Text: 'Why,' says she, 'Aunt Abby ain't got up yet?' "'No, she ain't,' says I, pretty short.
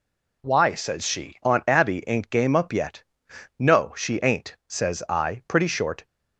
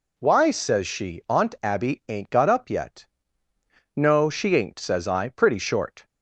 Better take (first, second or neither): second